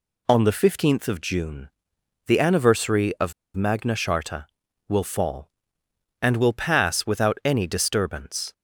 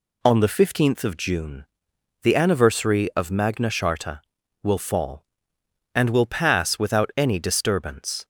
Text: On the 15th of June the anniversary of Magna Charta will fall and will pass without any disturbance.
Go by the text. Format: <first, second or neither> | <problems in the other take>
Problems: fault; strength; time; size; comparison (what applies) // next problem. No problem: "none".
second | pauses between "June" and "the"; noticeable; at 1.6 s; 0.56 s long; noticeable in the second // pauses between "of" and "Magna"; slight; at 3.3 s; 0.23 s long